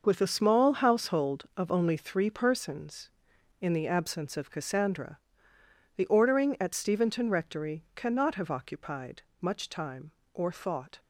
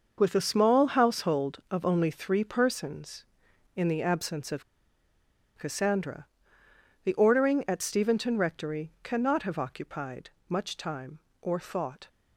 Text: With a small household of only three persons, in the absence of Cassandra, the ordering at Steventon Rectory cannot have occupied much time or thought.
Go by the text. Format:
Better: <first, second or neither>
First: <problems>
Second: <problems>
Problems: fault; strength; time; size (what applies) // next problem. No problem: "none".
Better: first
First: starts louder than the rest; noticeable; until 1.0 s; 6 dB // pauses between "occupied" and "much"; slight; at 9.2 s; 0.18 s long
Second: starts louder than the rest; noticeable; until 1.1 s; 6 dB // pauses between "of" and "Cassandra"; noticeable; at 4.6 s; 0.94 s long // pauses between "occupied" and "much"; slight; at 10.2 s; 0.18 s long